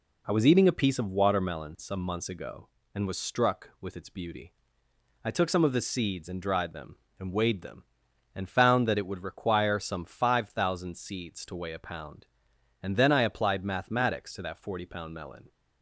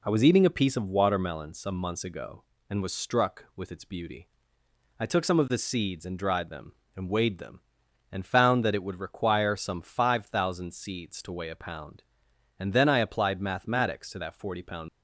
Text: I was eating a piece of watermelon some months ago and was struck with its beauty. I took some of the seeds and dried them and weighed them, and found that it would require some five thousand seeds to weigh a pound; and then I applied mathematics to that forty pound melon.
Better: first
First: none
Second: stops before "melon"; at 14.8 s

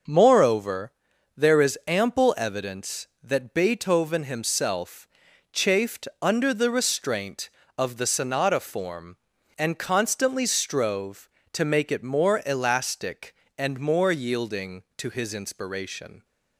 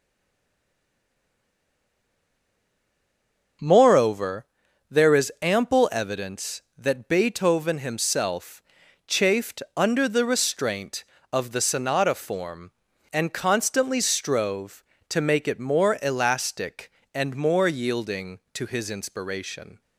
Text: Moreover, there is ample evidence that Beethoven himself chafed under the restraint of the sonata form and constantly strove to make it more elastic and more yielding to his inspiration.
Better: first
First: starts louder than the rest; noticeable; until 1.5 s; 6 dB // pauses between "himself" and "chafed"; at 5.0 s; 0.44 s long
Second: stays silent before the first word; strong; until 3.6 s; 3.6 s long // starts louder than the rest; noticeable; until 5.0 s; 6 dB // pauses between "himself" and "chafed"; at 8.6 s; 0.44 s long

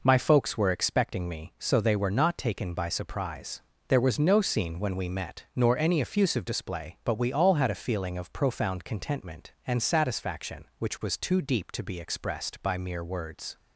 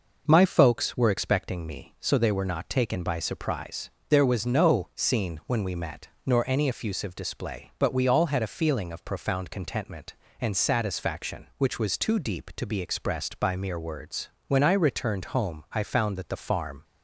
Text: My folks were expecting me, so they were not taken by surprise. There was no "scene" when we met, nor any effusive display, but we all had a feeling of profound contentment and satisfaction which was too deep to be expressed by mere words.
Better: first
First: none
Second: goes on to say "When I returned home I found that the farm"; strong; from 14.4 s on; 2.3 s long

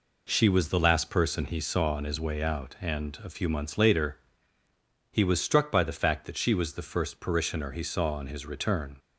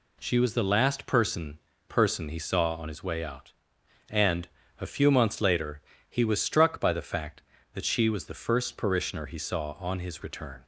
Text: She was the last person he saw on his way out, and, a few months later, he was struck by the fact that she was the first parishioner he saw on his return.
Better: first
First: none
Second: says "person" twice; at 1.8 s

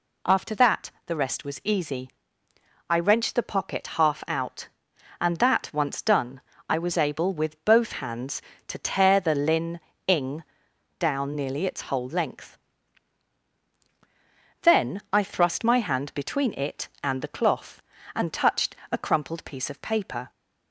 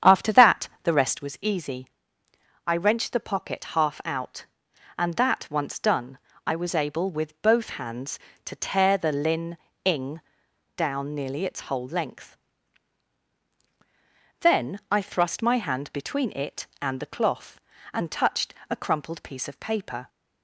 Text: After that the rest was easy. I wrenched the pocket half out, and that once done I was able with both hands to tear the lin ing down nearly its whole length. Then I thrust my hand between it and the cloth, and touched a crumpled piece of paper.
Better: first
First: pauses between "that" and "the"; slight; at 0.8 s; 0.16 s long // pauses between "done" and "I"; slight; at 6.4 s; 0.26 s long // pauses between "lin" and "ing"; slight; at 9.7 s; 0.28 s long // pauses between "ing" and "down"; noticeable; at 10.4 s; 0.54 s long // pauses between "touched" and "a"; slight; at 18.7 s; 0.16 s long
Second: starts louder than the rest; strong; until 1.3 s; 8.5 dB // pauses between "that" and "the"; slight; at 0.6 s; 0.16 s long // pauses between "done" and "I"; slight; at 6.1 s; 0.26 s long // pauses between "lin" and "ing"; slight; at 9.5 s; 0.28 s long // pauses between "ing" and "down"; noticeable; at 10.2 s; 0.54 s long // pauses between "touched" and "a"; slight; at 18.5 s; 0.16 s long

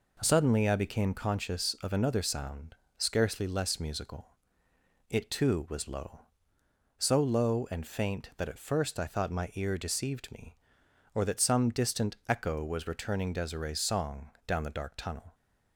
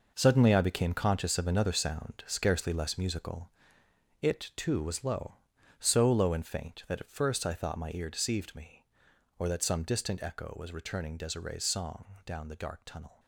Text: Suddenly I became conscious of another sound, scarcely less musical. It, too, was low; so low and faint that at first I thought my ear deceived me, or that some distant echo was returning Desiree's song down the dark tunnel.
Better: first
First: pauses between "song" and "down"; slight; at 14.3 s; 0.18 s long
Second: gets quieter; strong; throughout; 10 dB // pauses between "song" and "down"; slight; at 12.0 s; 0.20 s long

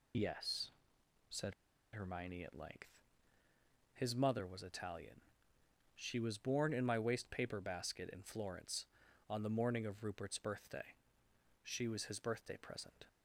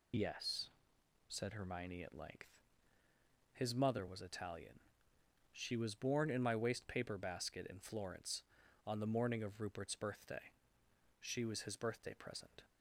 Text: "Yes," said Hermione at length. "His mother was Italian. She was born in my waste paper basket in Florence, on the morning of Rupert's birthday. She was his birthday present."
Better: second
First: pauses between "said" and "Hermione"; at 1.5 s; 0.42 s long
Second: none

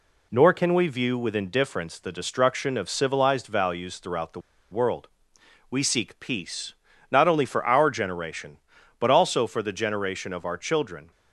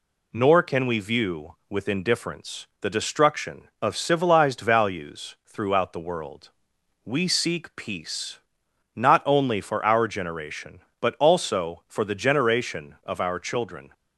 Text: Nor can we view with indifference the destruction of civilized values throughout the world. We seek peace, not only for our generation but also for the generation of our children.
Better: second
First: pauses between "the" and "world"; slight; at 4.3 s; 0.32 s long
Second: none

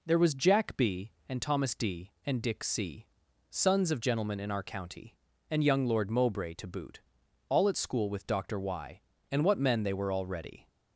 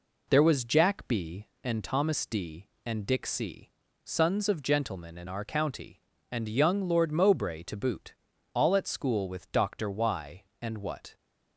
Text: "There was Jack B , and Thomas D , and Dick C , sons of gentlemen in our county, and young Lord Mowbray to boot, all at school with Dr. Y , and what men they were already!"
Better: first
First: none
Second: stops before "men they were already"; at 11.1 s

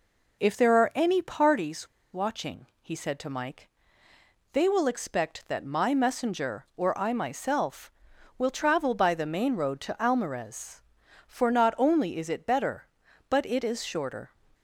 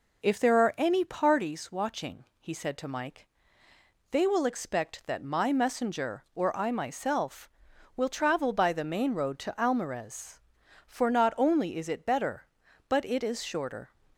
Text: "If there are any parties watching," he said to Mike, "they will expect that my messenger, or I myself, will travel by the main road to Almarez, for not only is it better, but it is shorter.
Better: second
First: pauses between "parties" and "watching"; slight; at 1.8 s; 0.24 s long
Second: none

